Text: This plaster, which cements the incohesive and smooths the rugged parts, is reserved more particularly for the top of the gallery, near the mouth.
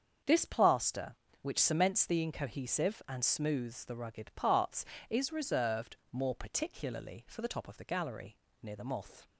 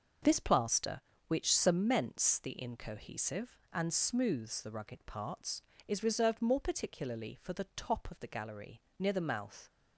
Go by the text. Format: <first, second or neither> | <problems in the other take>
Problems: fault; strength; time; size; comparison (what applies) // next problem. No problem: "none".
second | starts louder than the rest; until 1.4 s; 7 dB // pauses between "reserved" and "more"; slight; at 5.9 s; 0.16 s long // says "moth" for "mouth"; at 8.8 s